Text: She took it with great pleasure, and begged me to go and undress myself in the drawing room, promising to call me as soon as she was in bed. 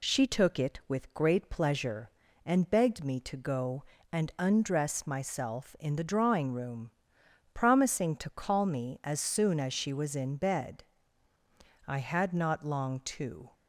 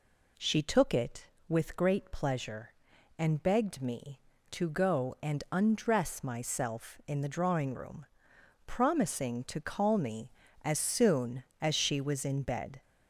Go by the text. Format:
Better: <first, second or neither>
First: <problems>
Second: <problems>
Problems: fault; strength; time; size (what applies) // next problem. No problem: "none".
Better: second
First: goes on to say "I had not long to"; from 11.8 s on; 1.6 s long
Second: none